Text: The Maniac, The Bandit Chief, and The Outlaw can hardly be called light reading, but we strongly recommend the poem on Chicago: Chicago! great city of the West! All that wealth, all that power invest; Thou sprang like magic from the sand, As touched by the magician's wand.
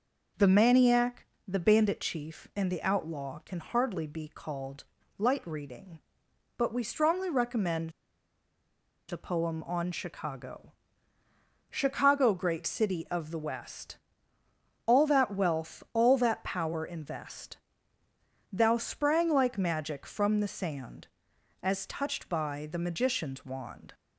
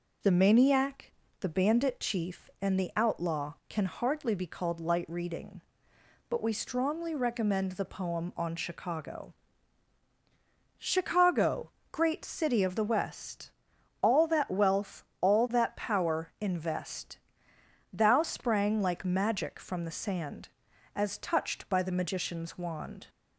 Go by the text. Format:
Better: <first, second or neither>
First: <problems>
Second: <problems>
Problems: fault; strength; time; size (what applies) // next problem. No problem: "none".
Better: second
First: pauses between "called" and "light"; slight; at 4.8 s; 0.34 s long // pauses between "recommend" and "the"; at 7.9 s; 1.1 s long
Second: none